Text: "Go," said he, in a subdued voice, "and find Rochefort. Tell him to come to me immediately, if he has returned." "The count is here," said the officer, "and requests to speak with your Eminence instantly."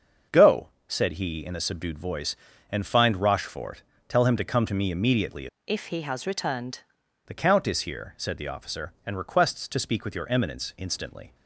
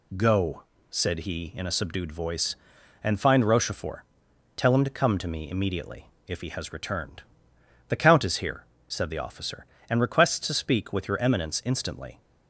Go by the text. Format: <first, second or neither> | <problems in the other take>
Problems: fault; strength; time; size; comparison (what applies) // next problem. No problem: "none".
second | starts louder than the rest; until 1.4 s; 6.5 dB // changes voice from "if" to "returned"; from 5.6 to 6.8 s; 1.2 s long